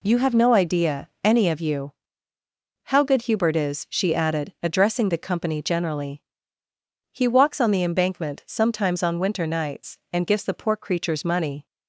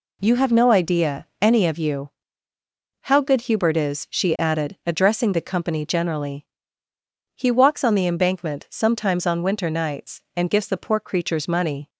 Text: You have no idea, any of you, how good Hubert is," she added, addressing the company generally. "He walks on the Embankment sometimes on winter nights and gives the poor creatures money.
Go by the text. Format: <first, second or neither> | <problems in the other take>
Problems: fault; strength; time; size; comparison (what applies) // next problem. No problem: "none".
neither | none